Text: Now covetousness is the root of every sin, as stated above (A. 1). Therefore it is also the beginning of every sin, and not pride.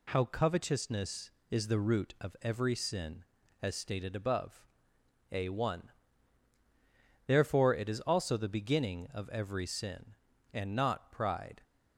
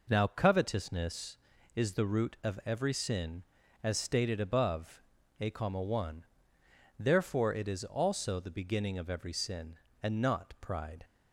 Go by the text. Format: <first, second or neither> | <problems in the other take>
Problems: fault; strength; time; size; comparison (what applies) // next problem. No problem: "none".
second | says "How" for "Now"; at 0.1 s